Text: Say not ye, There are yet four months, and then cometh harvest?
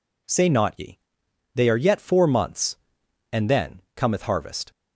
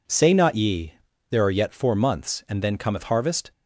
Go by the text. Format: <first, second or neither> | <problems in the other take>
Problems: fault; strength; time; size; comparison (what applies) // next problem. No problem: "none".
second | says "They" for "There"; at 1.5 s